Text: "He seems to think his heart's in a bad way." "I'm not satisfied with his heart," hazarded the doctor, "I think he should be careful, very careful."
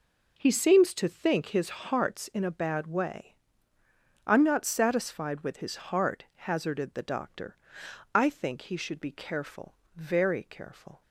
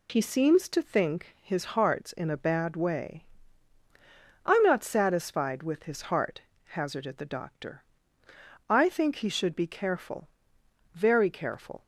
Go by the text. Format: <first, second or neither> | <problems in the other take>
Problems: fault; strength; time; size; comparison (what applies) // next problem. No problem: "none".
neither | none